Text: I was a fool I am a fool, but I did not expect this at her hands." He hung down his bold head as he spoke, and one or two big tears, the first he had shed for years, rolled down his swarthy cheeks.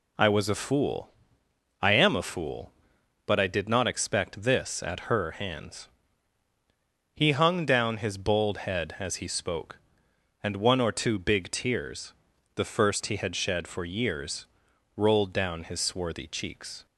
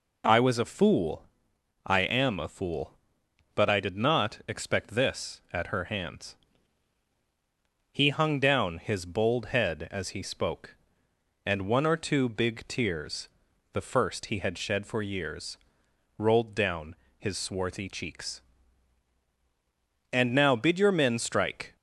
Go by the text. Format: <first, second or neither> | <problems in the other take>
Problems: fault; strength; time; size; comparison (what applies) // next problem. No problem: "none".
first | pauses between "fool" and "I"; noticeable; at 1.2 s; 0.62 s long; noticeable in the first // pauses between "down" and "his"; slight; at 16.9 s; 0.24 s long // goes on to say "And now bid your men strike"; from 20.1 s on; 1.6 s long